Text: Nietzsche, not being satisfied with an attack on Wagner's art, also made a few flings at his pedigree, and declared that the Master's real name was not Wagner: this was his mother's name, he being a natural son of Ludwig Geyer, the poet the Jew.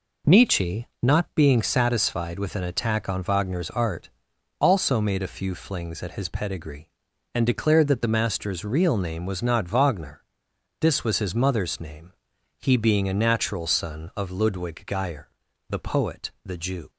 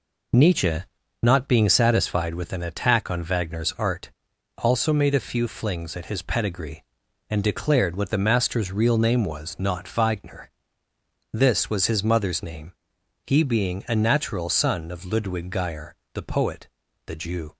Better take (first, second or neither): first